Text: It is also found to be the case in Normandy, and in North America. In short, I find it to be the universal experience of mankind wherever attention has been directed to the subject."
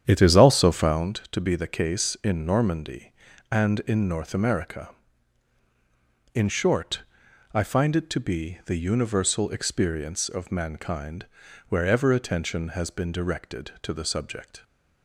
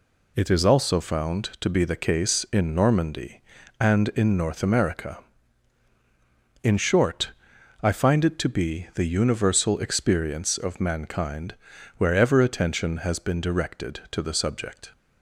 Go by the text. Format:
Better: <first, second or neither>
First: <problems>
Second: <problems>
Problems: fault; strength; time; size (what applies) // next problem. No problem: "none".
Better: second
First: starts louder than the rest; strong; until 1.1 s; 9 dB // pauses between "mankind" and "wherever"; at 11.2 s; 0.42 s long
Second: pauses between "mankind" and "wherever"; at 11.5 s; 0.42 s long